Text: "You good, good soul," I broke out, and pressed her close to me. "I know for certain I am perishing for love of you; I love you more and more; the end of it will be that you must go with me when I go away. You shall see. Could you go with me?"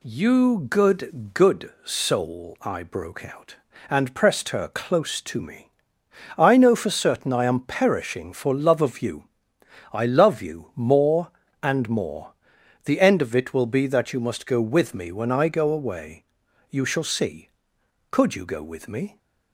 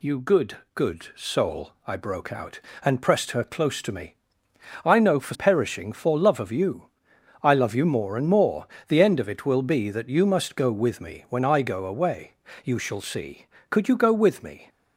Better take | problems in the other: first | skips "certain I am"; at 5.3 s

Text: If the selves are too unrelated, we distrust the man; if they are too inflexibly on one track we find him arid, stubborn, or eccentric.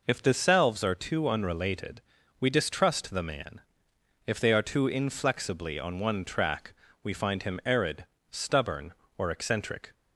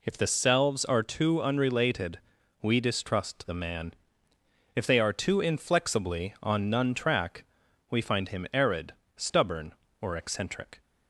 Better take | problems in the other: first | says "none" for "one"; at 6.7 s // pauses between "track" and "we"; noticeable; at 7.4 s; 0.46 s long; slight in the first

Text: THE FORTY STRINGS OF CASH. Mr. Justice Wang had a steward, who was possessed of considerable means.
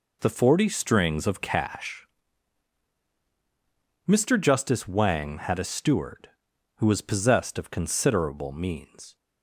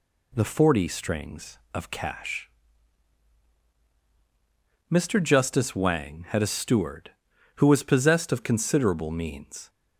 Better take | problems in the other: neither | none

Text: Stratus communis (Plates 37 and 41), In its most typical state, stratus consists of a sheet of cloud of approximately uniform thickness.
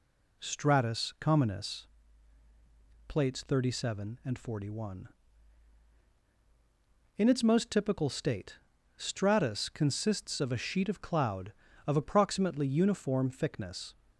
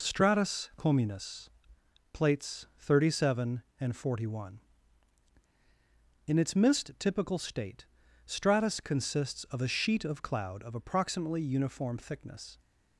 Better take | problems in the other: first | says "mist" for "most"; at 6.5 s

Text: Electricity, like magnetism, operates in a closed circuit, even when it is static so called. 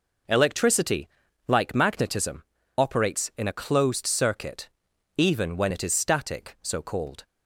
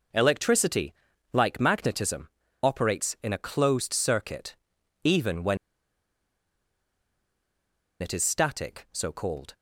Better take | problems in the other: first | pauses between "when" and "it"; strong; at 5.5 s; 2.4 s long

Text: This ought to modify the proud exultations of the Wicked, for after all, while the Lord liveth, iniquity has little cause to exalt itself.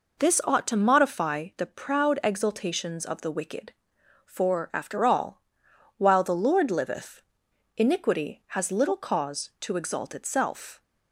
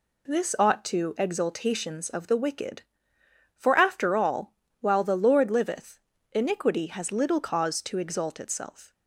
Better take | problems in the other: first | skips "modify the proud"; at 1.1 s

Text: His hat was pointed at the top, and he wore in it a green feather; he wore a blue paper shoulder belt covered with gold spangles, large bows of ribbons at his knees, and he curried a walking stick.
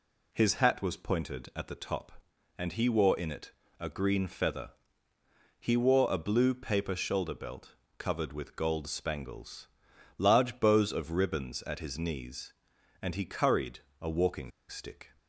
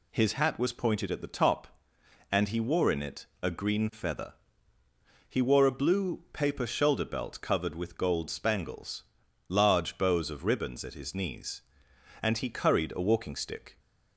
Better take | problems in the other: second | pauses between "it" and "a"; slight; at 3.5 s; 0.30 s long; slight in the second // pauses between "belt" and "covered"; slight; at 7.7 s; 0.22 s long // pauses between "curried" and "a"; slight; at 13.8 s; 0.20 s long // pauses between "walking" and "stick"; slight; at 14.5 s; 0.20 s long

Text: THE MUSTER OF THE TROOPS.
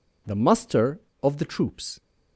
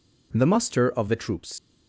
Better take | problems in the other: first | leaves "TROOPS" unfinished; at 1.5 s; 115 ms

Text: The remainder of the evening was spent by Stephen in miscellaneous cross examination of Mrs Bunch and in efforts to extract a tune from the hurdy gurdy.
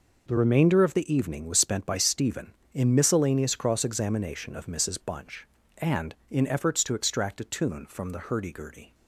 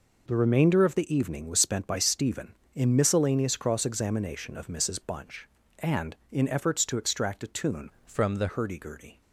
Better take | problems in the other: first | changes voice from "from" to "the"; from 8.0 to 8.4 s; 0.4 s long

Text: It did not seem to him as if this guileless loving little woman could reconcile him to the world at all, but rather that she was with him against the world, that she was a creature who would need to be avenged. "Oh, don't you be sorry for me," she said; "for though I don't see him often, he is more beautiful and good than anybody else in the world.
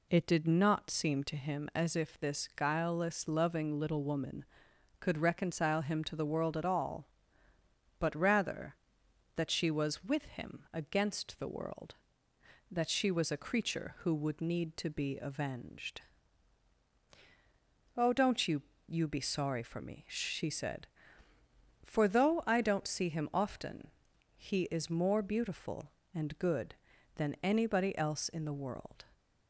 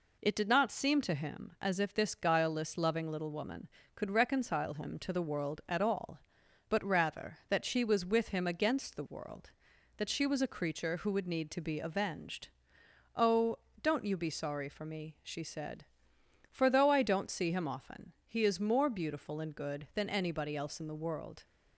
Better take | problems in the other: second | says "you" twice; at 18.8 s

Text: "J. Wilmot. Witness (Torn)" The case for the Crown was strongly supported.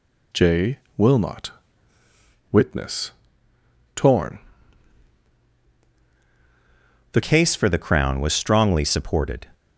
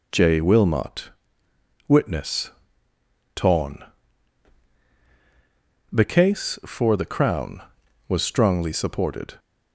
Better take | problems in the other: second | changes voice at "case"; from 7.2 s on; 2.2 s long

